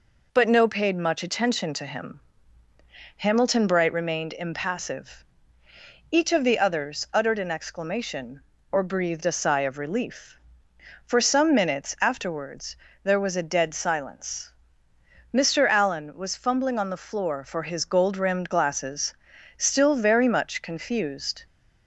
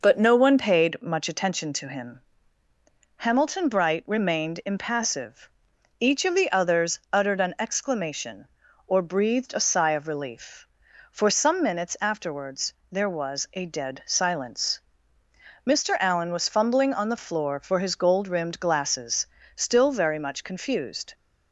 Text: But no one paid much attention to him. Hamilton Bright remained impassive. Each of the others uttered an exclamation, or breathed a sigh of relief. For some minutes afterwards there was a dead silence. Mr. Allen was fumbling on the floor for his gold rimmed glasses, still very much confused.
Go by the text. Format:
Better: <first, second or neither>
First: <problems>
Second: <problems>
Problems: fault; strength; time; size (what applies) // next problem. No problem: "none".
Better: second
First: skips "one"; at 0.6 s // pauses between "afterwards" and "there"; slight; at 12.7 s; 0.26 s long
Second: pauses between "afterwards" and "there"; slight; at 12.7 s; 0.18 s long